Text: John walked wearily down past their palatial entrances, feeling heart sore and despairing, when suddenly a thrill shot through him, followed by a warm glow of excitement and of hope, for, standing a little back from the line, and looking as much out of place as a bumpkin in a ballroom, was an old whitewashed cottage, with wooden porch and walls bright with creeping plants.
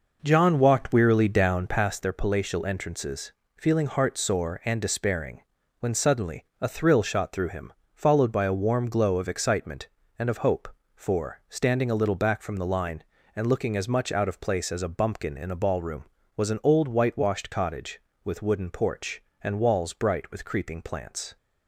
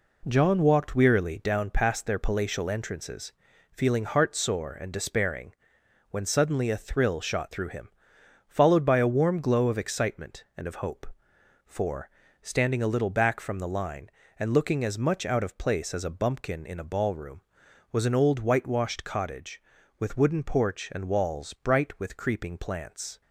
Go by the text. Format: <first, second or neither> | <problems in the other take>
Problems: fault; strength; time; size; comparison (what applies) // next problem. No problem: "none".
second | starts louder than the rest; noticeable; until 1.9 s; 5.5 dB // pauses between "suddenly" and "a"; slight; at 6.4 s; 0.16 s long